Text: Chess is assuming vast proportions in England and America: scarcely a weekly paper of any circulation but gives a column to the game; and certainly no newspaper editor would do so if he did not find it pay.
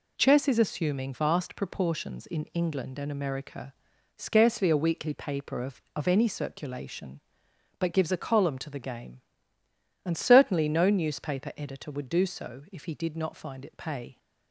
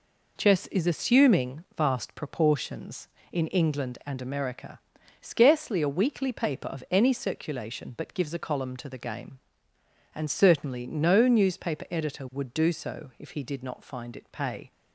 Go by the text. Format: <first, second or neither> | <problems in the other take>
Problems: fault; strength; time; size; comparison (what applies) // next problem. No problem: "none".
second | says "of" twice; at 5.9 s